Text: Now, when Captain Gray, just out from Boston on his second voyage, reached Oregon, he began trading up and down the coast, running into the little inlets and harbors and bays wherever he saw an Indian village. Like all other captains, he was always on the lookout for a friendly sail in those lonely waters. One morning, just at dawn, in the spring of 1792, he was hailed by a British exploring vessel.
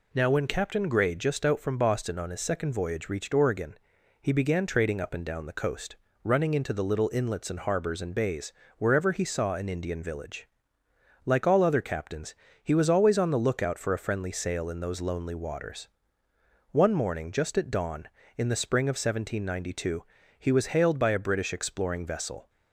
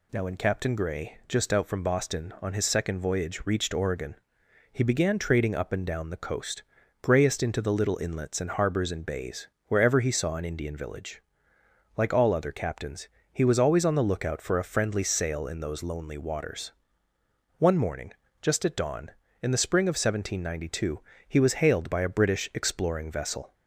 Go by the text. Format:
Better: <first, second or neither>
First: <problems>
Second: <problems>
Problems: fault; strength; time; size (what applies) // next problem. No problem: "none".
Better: first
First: pauses between "bays" and "wherever"; slight; at 8.5 s; 0.26 s long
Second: says "grayest" for "running"; at 7.0 s // pauses between "bays" and "wherever"; slight; at 9.4 s; 0.20 s long